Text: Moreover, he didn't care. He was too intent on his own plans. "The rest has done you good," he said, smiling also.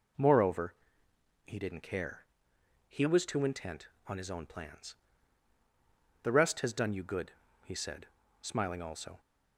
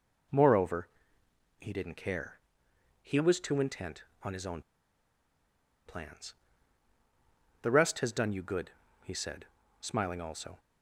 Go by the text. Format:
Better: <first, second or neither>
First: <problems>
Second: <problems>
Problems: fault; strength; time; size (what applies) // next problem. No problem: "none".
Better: first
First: none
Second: pauses between "own" and "plans"; strong; at 4.6 s; 1.2 s long